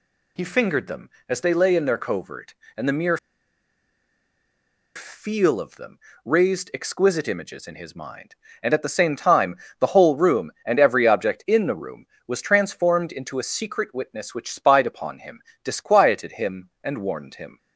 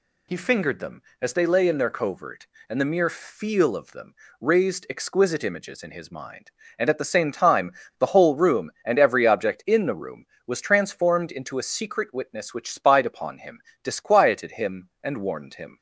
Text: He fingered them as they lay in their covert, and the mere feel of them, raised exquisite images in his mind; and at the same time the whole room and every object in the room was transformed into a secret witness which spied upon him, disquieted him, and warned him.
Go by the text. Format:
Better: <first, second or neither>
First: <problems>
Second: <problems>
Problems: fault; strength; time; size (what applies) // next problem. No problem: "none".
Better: second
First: pauses between "mere" and "feel"; strong; at 3.1 s; 1.7 s long // pauses between "time" and "the"; slight; at 9.5 s; 0.24 s long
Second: pauses between "time" and "the"; slight; at 7.7 s; 0.27 s long